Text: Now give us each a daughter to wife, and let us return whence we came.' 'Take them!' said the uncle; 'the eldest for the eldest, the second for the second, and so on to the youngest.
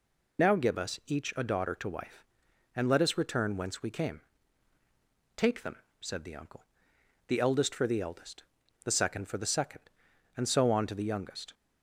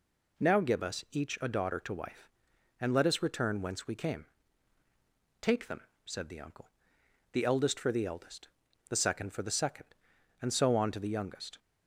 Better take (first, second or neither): second